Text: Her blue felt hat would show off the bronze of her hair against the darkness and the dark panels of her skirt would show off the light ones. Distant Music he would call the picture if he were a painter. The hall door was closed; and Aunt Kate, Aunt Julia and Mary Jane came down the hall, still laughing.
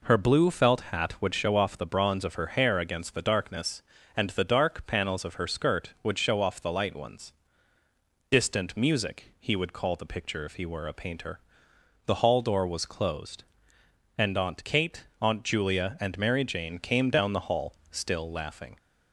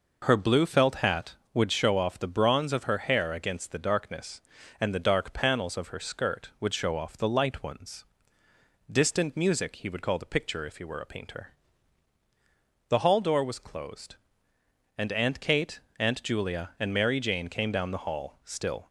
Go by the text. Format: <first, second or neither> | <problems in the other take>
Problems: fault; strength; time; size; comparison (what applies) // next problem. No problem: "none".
first | stops before "laughing"; at 18.8 s